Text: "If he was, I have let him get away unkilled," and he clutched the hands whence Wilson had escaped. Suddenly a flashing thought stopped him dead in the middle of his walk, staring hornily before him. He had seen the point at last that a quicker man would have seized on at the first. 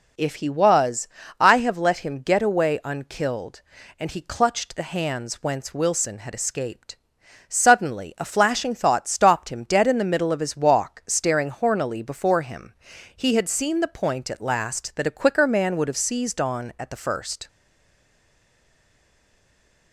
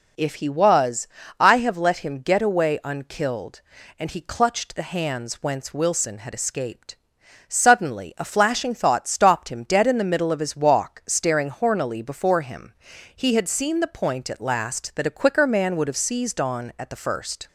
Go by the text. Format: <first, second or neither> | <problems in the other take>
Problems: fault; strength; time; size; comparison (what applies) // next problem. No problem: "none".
second | stays silent after the last word; from 17.4 s on; 2.5 s long